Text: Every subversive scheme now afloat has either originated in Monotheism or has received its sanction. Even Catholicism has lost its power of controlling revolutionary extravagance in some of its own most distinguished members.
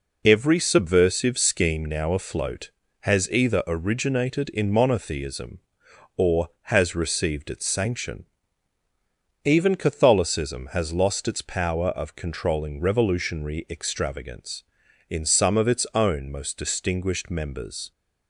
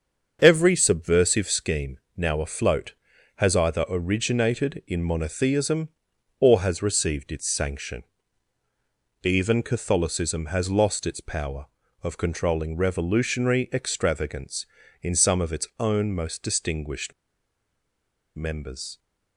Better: first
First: none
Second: starts louder than the rest; until 1.4 s; 7 dB // pauses between "scheme" and "now"; slight; at 1.9 s; 0.18 s long // pauses between "distinguished" and "members"; at 17.1 s; 1.2 s long

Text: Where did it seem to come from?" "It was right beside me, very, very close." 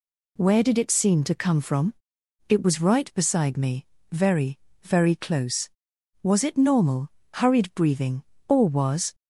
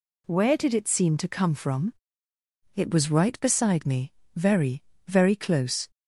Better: second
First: goes on to say "Was it normal hurried breathing or was"; strong; from 6.2 s on; 2.9 s long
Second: none

